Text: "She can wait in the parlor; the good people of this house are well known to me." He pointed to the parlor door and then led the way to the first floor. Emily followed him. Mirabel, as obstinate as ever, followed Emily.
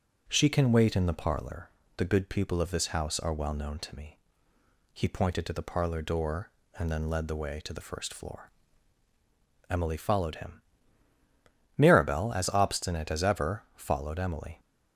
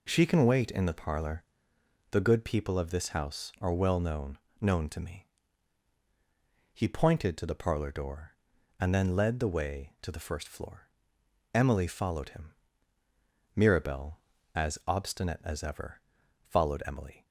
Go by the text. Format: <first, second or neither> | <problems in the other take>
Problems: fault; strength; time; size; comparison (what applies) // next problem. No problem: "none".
first | says "known" twice; at 4.6 s